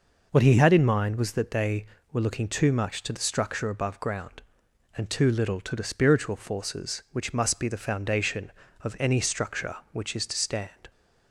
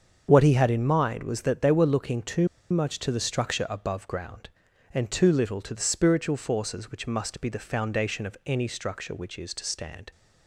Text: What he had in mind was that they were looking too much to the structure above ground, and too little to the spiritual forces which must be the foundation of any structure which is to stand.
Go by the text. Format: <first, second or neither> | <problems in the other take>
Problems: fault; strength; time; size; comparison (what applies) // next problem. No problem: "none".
first | starts louder than the rest; until 1.3 s; 7 dB // pauses between "too" and "much"; slight; at 2.4 s; 0.23 s long